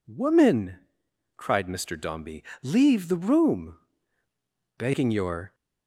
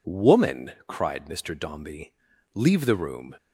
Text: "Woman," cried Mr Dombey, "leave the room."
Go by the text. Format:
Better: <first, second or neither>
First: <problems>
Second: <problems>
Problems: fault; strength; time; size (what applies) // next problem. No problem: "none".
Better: second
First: goes on to say "Begging your"; noticeable; from 4.7 s on; 0.78 s long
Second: none